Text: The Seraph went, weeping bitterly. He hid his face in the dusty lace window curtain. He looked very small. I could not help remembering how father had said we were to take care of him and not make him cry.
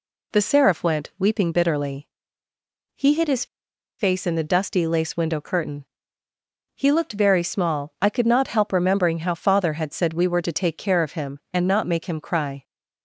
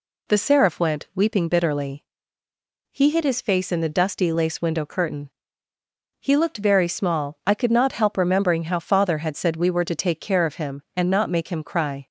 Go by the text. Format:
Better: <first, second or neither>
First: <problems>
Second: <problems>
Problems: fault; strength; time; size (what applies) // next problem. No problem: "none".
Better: second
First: pauses between "his" and "face"; noticeable; at 3.4 s; 0.52 s long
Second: none